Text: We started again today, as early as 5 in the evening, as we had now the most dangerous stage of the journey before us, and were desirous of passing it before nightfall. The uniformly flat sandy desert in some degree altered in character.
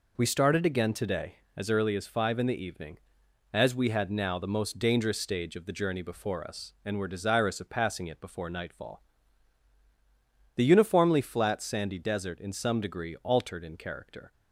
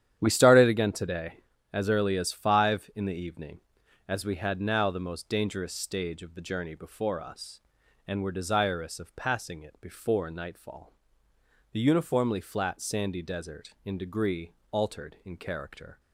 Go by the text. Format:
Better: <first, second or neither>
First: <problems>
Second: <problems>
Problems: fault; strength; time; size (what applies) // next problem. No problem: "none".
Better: first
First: none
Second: starts louder than the rest; strong; until 1.2 s; 10 dB // skips "some"; at 13.9 s // pauses between "degree" and "altered"; slight; at 14.5 s; 0.18 s long